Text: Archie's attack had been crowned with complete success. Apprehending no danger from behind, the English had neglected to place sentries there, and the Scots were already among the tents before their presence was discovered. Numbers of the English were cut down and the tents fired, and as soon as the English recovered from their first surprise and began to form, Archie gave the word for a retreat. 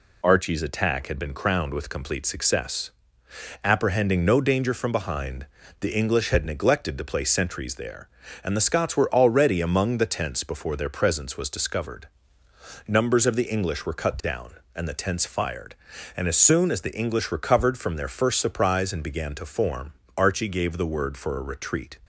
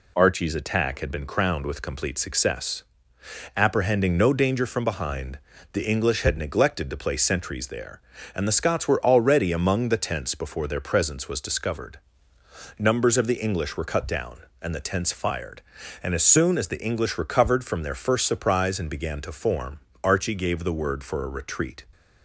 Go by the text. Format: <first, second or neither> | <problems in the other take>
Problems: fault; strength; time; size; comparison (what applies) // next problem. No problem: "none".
neither | none